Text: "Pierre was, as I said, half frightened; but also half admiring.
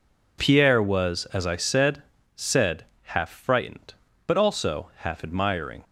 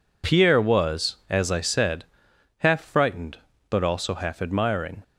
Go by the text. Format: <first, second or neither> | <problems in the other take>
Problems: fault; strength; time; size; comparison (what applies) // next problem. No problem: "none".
second | says "said" twice; at 2.3 s